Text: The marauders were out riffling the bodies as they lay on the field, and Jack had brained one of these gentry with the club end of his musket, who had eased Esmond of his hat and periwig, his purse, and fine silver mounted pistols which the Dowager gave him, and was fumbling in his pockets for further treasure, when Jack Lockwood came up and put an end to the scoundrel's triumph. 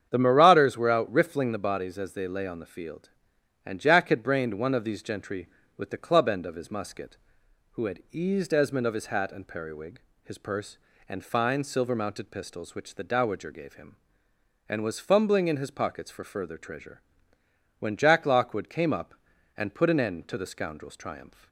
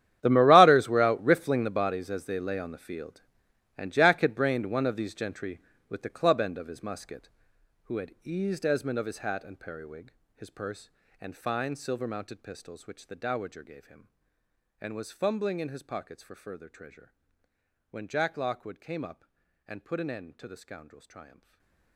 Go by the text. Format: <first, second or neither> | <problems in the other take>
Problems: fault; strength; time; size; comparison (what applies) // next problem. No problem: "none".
first | gets quieter; strong; throughout; 18.5 dB // starts louder than the rest; strong; until 1.2 s; 11 dB; strong in the first // stays silent after the last word; slight; from 21.2 s on; 0.7 s long